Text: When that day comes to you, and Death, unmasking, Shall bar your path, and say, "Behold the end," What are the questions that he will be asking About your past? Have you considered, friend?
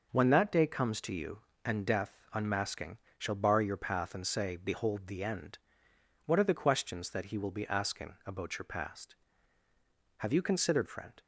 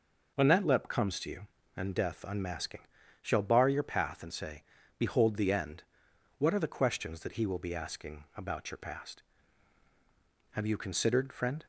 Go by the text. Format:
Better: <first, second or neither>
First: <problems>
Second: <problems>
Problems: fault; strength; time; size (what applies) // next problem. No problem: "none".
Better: first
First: none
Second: says "lep" for "day"; at 0.6 s